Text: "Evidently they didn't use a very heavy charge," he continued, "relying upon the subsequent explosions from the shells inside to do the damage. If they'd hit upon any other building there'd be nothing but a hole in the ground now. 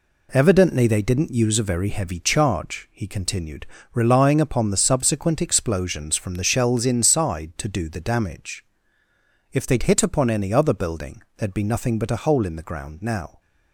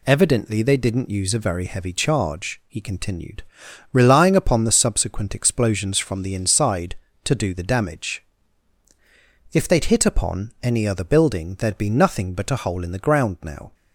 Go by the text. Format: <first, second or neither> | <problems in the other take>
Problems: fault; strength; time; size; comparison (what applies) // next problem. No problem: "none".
first | skips "shells"; at 6.3 s